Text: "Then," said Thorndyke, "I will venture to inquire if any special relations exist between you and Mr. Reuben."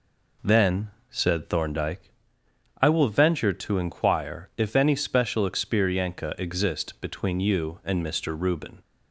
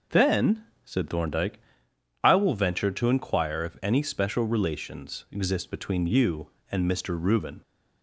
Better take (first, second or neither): second